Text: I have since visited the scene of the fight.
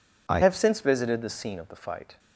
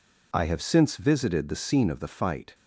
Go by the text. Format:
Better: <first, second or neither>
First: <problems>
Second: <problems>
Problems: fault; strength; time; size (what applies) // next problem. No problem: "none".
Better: second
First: changes voice at "have"; from 0.4 s on; 1.7 s long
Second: none